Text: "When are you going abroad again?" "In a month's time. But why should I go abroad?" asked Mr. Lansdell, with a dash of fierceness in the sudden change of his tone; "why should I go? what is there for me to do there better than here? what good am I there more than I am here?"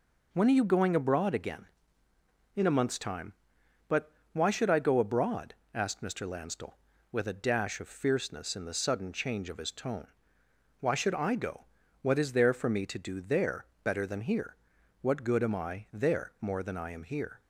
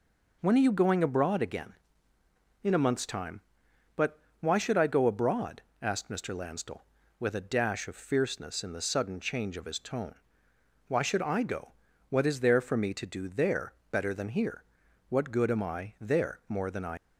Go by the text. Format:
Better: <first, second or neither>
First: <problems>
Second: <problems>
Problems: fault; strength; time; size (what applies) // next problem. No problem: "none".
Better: first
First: pauses between "But" and "why"; slight; at 4.1 s; 0.22 s long // pauses between "there" and "better"; slight; at 13.6 s; 0.18 s long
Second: pauses between "But" and "why"; slight; at 4.1 s; 0.22 s long // pauses between "there" and "better"; slight; at 13.7 s; 0.18 s long // stops before "am here"; at 16.9 s